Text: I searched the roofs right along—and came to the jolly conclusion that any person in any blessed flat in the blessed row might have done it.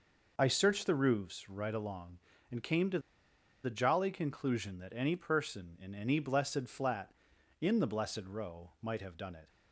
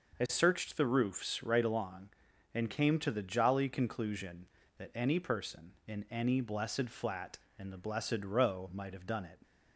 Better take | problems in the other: second | pauses between "to" and "the"; noticeable; at 2.9 s; 0.64 s long

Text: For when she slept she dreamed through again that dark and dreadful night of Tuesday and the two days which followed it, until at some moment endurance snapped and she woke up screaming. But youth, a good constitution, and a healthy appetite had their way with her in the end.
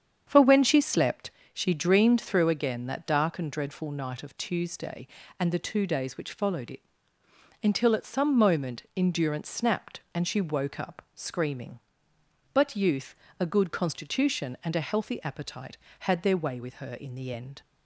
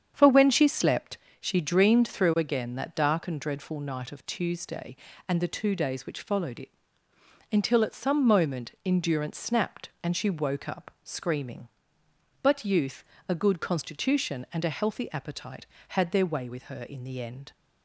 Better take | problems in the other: neither | starts louder than the rest; strong; the same in both // pauses between "slept" and "she"; slight; the same in both

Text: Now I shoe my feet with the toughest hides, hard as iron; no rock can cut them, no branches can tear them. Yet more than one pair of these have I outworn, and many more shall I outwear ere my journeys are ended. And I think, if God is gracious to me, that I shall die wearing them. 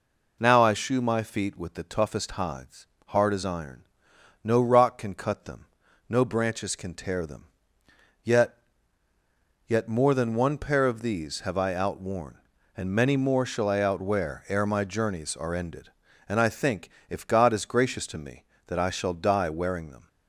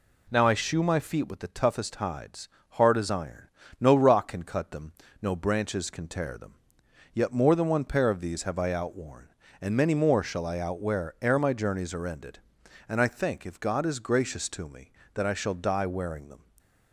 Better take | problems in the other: second | says "Yet" twice; at 9.6 s

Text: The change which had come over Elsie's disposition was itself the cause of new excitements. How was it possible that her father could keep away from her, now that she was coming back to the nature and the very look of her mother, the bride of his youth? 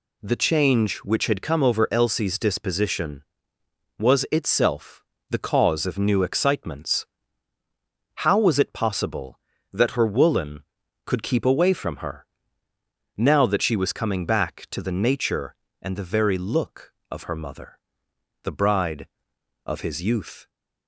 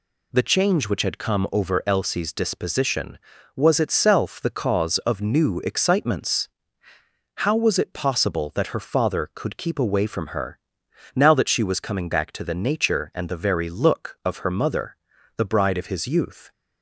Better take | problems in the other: second | pauses between "itself" and "the"; slight; at 5.0 s; 0.28 s long // says "woolen" for "father"; at 10.0 s

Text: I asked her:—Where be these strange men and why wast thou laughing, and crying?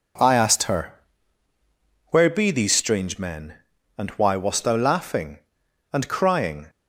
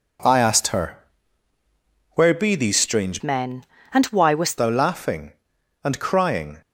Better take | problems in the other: first | changes voice from "men" to "wast"; from 3.2 to 4.5 s; 1.3 s long

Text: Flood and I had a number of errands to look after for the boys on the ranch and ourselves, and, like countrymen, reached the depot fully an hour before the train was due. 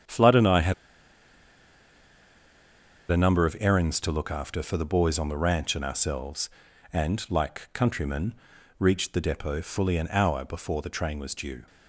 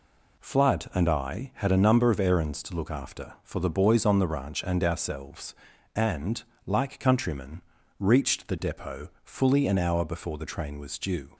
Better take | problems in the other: second | starts louder than the rest; strong; until 3.4 s; 8.5 dB // pauses between "had" and "a"; strong; at 0.7 s; 2.3 s long

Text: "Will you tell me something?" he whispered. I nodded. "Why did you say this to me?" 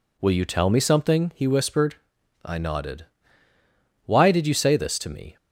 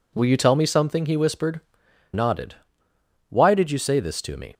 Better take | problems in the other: first | skips "I"; at 1.8 s

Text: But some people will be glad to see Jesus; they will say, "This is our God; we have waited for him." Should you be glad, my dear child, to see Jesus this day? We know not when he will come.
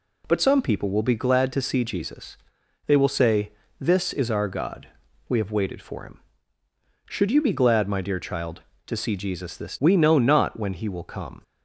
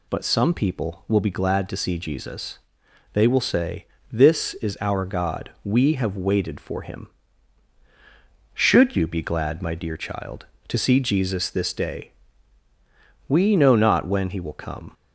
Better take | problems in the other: second | skips "day"; at 9.7 s

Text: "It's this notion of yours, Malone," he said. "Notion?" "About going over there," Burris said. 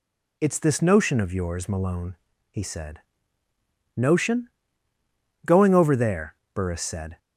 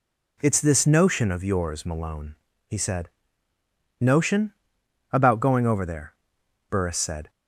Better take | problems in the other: second | skips "About"; at 4.9 s

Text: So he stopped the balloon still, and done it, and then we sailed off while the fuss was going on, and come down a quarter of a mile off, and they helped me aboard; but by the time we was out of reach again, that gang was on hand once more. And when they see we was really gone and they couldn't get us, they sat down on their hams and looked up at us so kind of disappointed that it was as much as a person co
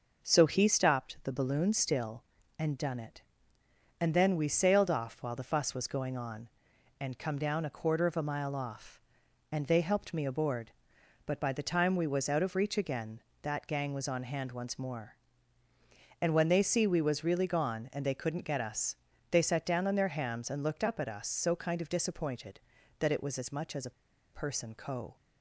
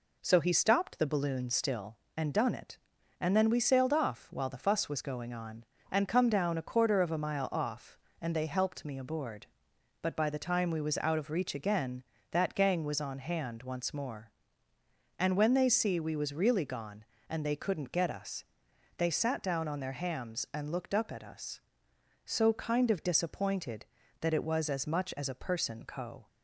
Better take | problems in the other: second | pauses between "a" and "person"; at 23.9 s; 0.42 s long

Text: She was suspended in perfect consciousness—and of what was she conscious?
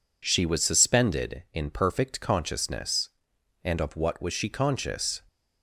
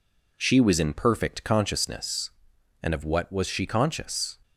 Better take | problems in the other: first | skips "suspended"; at 0.7 s

